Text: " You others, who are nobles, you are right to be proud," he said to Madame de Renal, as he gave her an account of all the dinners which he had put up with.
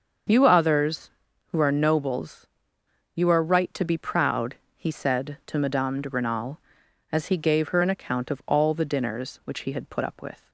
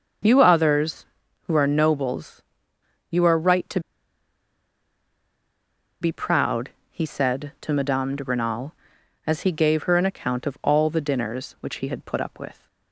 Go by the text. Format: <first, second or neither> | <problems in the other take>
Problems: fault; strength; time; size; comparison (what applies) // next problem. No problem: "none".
first | starts louder than the rest; until 1.6 s; 7 dB; also in the first // pauses between "to" and "be"; strong; at 3.7 s; 2.2 s long